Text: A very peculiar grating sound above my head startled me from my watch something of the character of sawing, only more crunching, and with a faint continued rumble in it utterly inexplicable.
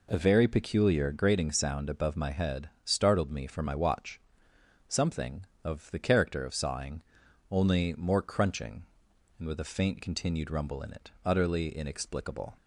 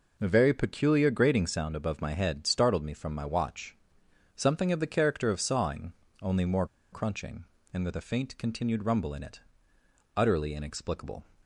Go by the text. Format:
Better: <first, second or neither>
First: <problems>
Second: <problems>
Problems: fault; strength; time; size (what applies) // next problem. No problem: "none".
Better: first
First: pauses between "watch" and "something"; noticeable; at 4.2 s; 0.66 s long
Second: pauses between "watch" and "something"; noticeable; at 3.7 s; 0.60 s long // pauses between "more" and "crunching"; slight; at 6.6 s; 0.24 s long // pauses between "it" and "utterly"; noticeable; at 9.3 s; 0.76 s long